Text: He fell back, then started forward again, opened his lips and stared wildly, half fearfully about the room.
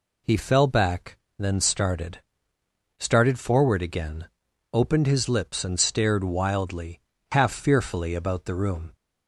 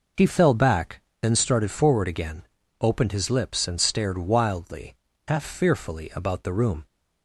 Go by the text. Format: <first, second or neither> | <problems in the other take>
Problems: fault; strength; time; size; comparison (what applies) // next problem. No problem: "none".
second | says "started" twice; at 2.9 s